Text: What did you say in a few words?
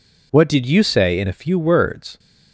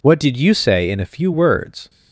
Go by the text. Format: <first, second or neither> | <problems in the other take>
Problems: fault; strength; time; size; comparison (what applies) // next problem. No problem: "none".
neither | none